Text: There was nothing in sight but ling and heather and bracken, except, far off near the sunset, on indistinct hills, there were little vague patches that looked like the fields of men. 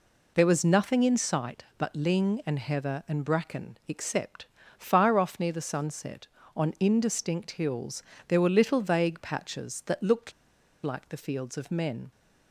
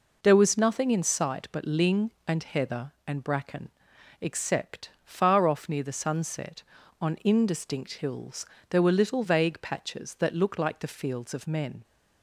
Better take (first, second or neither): second